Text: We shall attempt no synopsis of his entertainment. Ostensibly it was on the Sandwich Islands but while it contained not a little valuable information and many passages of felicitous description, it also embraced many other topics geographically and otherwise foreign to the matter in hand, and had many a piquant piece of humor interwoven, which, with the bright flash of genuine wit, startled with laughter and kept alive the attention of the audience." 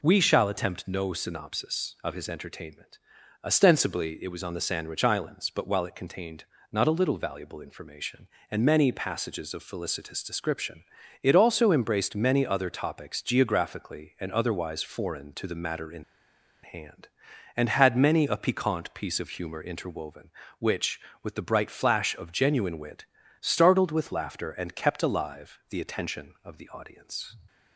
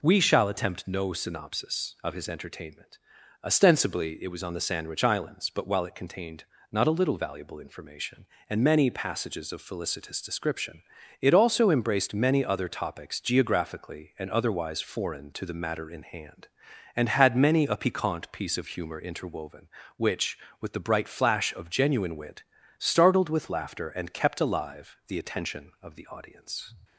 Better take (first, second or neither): second